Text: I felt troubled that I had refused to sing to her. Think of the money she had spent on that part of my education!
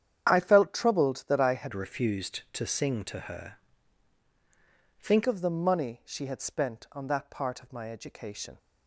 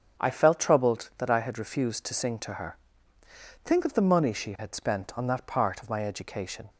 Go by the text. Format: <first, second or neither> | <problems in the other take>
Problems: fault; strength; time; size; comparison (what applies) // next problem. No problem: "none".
second | starts louder than the rest; strong; until 1.3 s; 9 dB; strong in the second // changes voice from "refused" to "Think"; from 1.7 to 5.2 s; 3.5 s long